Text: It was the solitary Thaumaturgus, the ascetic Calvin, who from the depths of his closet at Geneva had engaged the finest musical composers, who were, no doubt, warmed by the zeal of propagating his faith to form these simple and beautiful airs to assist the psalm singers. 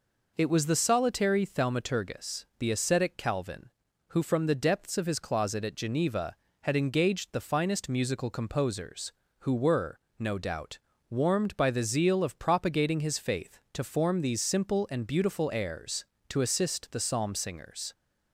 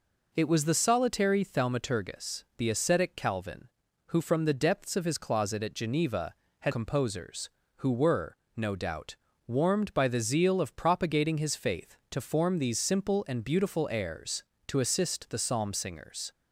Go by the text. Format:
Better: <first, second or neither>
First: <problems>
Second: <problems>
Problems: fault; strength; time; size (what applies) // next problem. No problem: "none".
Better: first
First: none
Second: skips "engaged the finest musical"; at 6.7 s